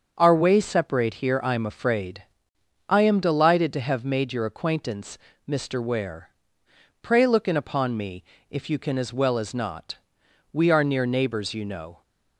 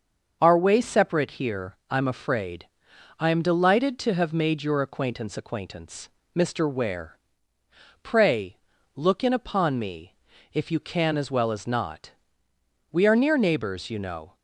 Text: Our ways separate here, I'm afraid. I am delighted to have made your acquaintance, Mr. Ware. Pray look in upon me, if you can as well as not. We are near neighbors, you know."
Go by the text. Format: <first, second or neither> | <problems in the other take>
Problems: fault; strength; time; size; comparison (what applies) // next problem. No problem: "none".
first | starts louder than the rest; until 1.4 s; 6.5 dB; also in the first // says "acquaintance" twice; at 5.3 s // pauses between "Pray" and "look"; at 8.5 s; 0.40 s long